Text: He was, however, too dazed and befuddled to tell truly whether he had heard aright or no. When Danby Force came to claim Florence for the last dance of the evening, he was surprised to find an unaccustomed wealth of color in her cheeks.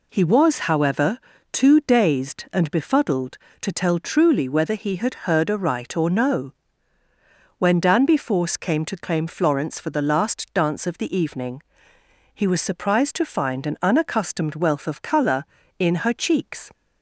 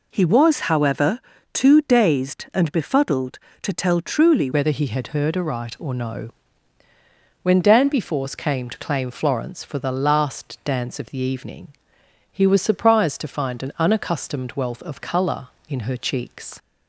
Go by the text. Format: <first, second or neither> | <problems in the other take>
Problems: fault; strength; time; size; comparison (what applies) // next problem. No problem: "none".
first | changes voice at "whether"; from 4.5 s on; 12.0 s long